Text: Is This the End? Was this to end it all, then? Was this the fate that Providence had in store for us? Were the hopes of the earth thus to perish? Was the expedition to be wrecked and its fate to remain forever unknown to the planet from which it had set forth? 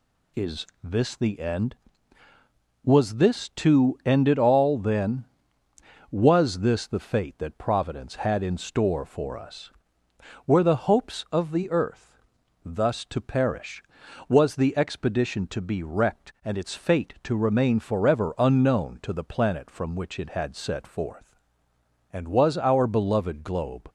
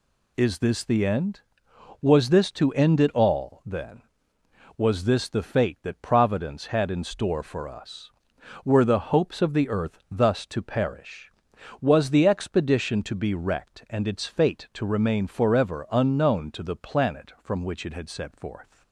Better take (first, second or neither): second